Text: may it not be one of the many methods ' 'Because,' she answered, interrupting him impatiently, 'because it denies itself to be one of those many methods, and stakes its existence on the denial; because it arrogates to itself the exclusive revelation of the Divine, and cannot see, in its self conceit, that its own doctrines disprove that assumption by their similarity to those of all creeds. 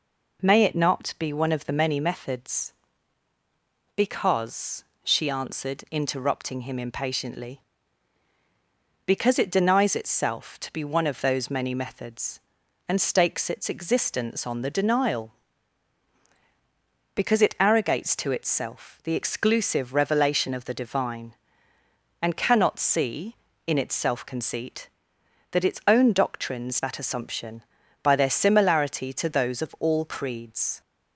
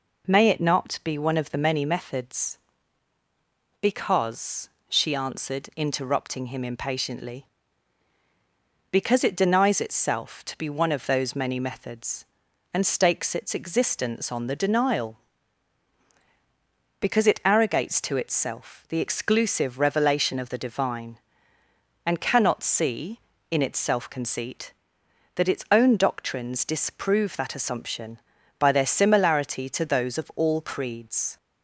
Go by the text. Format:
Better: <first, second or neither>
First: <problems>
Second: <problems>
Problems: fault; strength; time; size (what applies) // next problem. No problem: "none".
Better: second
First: skips "disprove"; at 26.8 s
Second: none